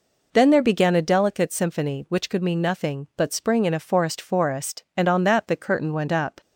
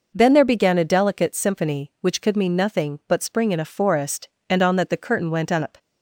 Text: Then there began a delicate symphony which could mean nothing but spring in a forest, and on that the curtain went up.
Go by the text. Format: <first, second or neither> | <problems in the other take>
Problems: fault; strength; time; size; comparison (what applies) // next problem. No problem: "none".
second | says "forest" twice; at 4.2 s